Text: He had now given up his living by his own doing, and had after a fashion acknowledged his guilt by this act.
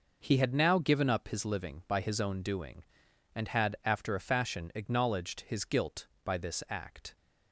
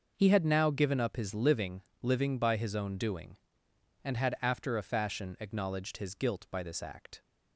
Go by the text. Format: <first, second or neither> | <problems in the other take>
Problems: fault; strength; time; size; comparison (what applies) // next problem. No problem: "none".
first | says "living" twice; at 2.0 s